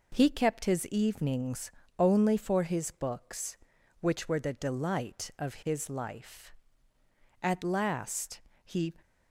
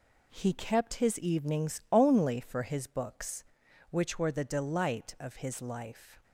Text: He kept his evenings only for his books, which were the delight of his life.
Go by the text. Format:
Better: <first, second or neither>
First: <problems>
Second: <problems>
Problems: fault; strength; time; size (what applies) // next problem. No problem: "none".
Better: second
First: pauses between "evenings" and "only"; slight; at 1.7 s; 0.26 s long // goes on to say "At last he"; from 7.4 s on; 1.5 s long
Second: none